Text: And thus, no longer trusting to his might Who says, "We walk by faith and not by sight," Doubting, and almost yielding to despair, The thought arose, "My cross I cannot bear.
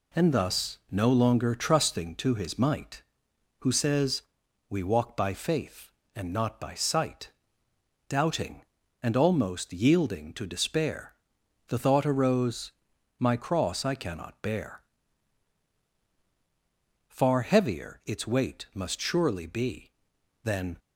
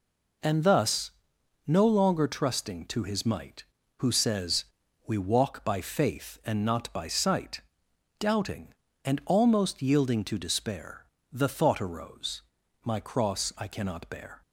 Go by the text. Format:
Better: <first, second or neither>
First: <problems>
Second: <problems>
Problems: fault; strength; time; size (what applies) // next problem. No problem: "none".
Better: second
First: goes on to say "Far heavier its weight must surely be Than"; strong; from 17.0 s on; 3.7 s long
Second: none